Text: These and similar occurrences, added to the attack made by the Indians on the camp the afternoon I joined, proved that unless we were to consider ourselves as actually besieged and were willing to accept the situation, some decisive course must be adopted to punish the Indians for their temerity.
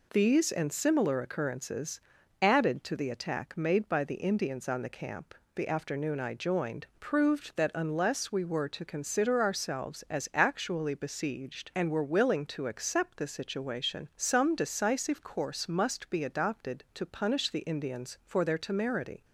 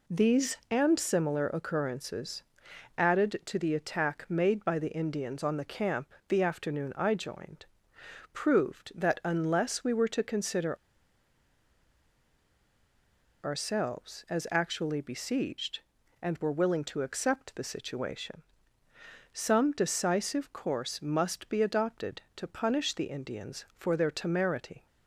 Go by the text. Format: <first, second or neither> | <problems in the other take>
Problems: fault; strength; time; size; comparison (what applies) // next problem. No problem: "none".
first | pauses between "camp" and "the"; slight; at 6.1 s; 0.16 s long; slight in the first // pauses between "consider" and "ourselves"; strong; at 10.7 s; 2.6 s long